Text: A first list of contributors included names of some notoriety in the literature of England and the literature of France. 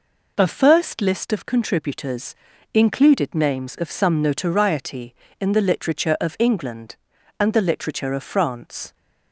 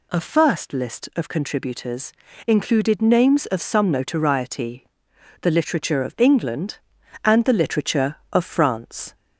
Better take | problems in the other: first | pauses between "contributors" and "included"; slight; at 2.1 s; 0.34 s long; also in the first // skips "in"; at 5.1 s

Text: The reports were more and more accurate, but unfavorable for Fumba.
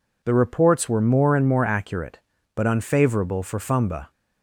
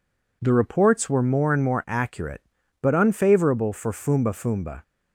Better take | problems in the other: first | says "Fumba" twice; at 4.3 s

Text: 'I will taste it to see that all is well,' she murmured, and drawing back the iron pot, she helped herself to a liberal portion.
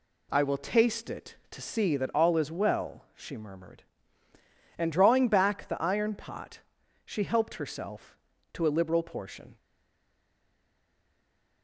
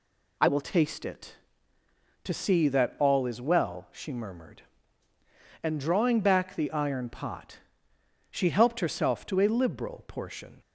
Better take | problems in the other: second | stays silent after the last word; noticeable; from 9.5 s on; 2.1 s long

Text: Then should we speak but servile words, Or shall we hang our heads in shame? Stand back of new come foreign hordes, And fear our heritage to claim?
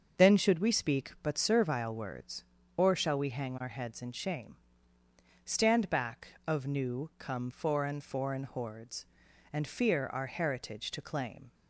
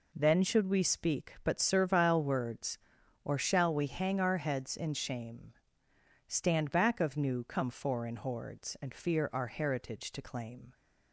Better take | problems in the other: second | starts louder than the rest; until 1.2 s; 6.5 dB // says "foreign" twice; at 7.9 s

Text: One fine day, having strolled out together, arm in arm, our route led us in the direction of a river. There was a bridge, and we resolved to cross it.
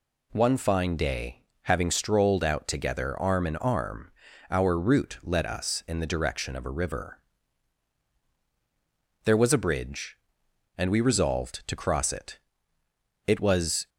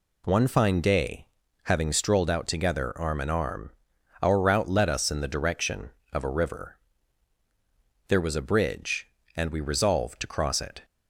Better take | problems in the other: second | goes on to say "It was"; noticeable; from 13.2 s on; 0.62 s long

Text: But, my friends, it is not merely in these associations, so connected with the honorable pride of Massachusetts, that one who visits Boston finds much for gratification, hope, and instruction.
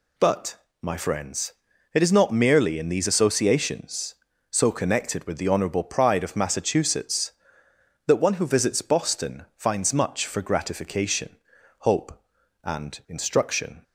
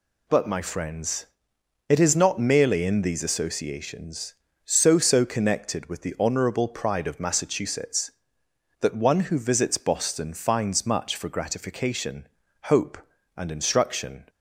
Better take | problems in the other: first | says "so" twice; at 4.9 s

